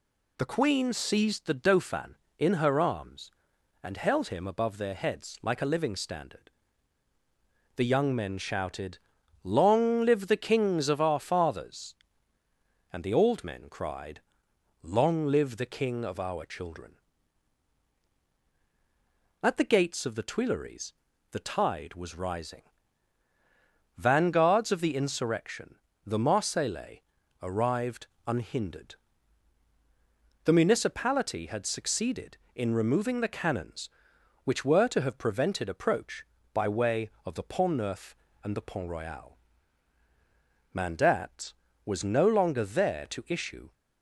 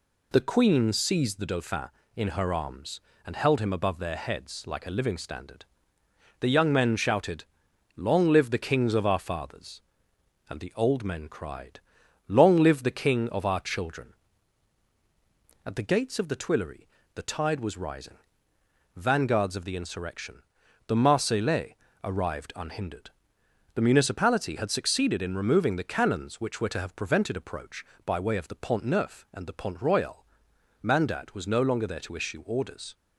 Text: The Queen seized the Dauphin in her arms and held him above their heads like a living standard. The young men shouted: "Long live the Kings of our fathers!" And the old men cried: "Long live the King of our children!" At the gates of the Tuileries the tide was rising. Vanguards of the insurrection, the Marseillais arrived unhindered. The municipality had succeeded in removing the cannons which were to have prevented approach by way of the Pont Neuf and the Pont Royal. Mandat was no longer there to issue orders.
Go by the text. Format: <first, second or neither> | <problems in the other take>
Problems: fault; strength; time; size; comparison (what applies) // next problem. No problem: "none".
second | pauses between "Tuileries" and "the"; at 20.9 s; 0.38 s long; slight in the second // pauses between "Marseillais" and "arrived"; at 27.0 s; 0.38 s long; slight in the second // pauses between "arrived" and "unhindered"; slight; at 28.0 s; 0.18 s long // stops before "orders"; at 43.7 s